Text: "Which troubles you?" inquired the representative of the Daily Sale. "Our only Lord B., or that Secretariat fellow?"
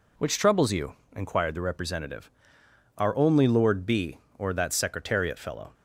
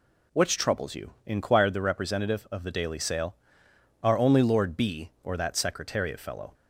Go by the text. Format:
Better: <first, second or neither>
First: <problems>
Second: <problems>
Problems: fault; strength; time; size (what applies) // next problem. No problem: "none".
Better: second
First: skips "of the Daily Sale"; at 2.6 s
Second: none